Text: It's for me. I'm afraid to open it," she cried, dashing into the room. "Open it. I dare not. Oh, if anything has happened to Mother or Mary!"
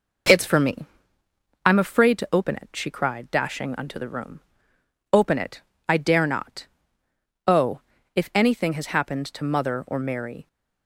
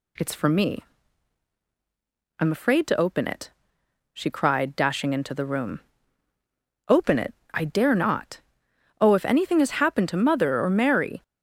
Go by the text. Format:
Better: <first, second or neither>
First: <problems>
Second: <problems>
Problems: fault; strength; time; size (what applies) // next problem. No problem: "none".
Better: second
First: says "unto" for "into"; at 3.7 s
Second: none